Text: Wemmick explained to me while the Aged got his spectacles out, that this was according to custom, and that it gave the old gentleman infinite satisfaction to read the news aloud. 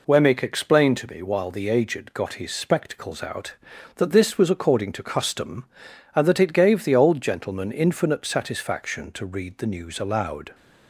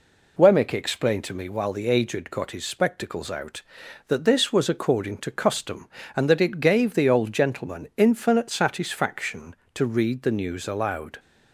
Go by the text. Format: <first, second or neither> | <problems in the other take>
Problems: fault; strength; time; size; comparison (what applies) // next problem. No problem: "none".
second | gets quieter; throughout; 3.5 dB